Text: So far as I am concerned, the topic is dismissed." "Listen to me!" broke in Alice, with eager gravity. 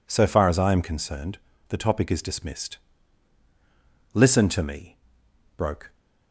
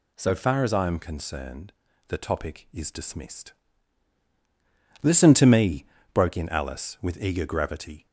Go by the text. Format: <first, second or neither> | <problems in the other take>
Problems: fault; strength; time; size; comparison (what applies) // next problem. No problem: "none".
second | stops before "in Alice with eager gravity"; at 5.9 s